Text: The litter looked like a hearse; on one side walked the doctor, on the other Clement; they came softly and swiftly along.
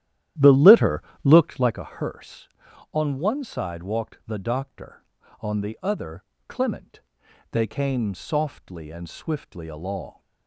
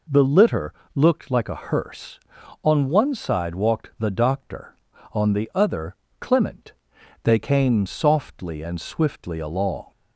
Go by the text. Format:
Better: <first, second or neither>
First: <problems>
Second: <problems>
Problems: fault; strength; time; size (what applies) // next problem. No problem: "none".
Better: second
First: starts louder than the rest; strong; until 1.9 s; 12 dB // pauses between "litter" and "looked"; slight; at 1.0 s; 0.22 s long // pauses between "other" and "Clement"; slight; at 6.2 s; 0.26 s long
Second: pauses between "litter" and "looked"; slight; at 0.7 s; 0.22 s long // pauses between "other" and "Clement"; slight; at 5.9 s; 0.26 s long